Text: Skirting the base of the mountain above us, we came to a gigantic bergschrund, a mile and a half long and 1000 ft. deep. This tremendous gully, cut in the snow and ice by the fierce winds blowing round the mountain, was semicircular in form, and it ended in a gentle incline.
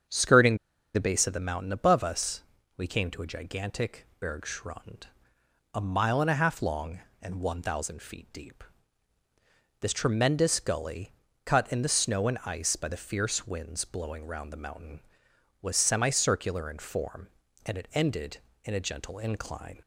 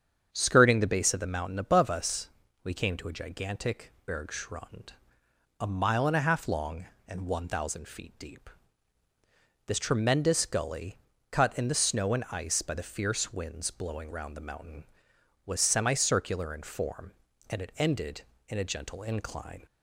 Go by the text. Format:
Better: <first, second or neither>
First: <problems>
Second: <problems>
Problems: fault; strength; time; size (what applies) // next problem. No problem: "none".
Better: second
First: starts louder than the rest; strong; until 1.4 s; 7.5 dB // pauses between "Skirting" and "the"; at 0.5 s; 0.39 s long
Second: starts louder than the rest; strong; until 1.3 s; 7.5 dB